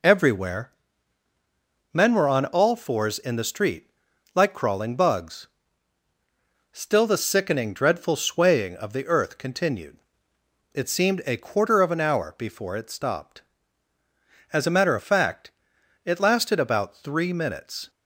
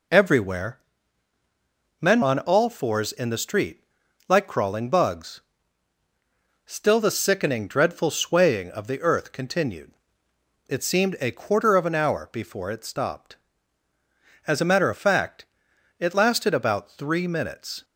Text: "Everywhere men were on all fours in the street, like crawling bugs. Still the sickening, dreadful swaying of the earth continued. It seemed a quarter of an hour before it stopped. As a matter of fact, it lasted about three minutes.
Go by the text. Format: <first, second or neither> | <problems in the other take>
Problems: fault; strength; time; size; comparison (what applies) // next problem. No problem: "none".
first | pauses between "Everywhere" and "men"; at 0.8 s; 1.2 s long; also in the first // skips "were"; at 2.2 s